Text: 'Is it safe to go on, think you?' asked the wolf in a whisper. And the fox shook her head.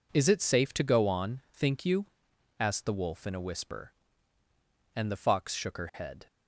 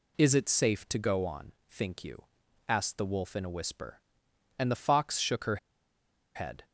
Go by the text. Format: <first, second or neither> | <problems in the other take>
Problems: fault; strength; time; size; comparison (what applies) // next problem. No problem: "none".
first | pauses between "her" and "head"; noticeable; at 5.5 s; 0.78 s long